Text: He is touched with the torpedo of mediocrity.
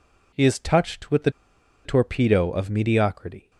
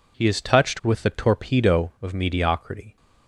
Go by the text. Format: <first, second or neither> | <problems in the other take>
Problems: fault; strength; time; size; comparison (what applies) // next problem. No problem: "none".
second | pauses between "the" and "torpedo"; noticeable; at 1.2 s; 0.55 s long